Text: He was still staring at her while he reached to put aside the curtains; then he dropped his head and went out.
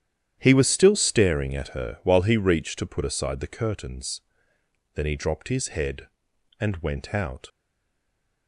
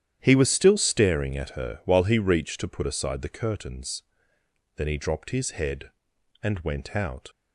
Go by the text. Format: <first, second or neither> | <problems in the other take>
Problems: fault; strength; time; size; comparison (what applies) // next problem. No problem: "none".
second | starts louder than the rest; strong; until 1.4 s; 10.5 dB; strong in the second // stays silent after the last word; from 7.4 s on; 1.0 s long